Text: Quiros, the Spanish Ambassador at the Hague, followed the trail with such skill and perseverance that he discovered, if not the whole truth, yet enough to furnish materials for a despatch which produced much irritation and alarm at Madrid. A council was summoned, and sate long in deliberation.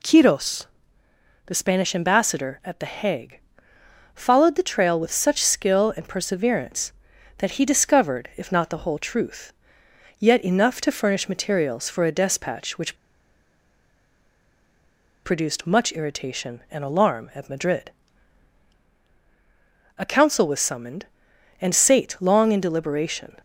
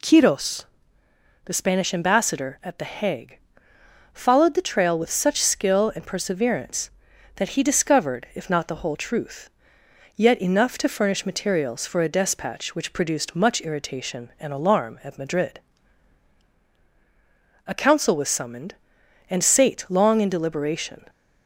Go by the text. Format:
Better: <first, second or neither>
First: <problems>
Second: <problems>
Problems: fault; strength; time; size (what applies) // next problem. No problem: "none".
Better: second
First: pauses between "which" and "produced"; strong; at 12.9 s; 2.2 s long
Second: none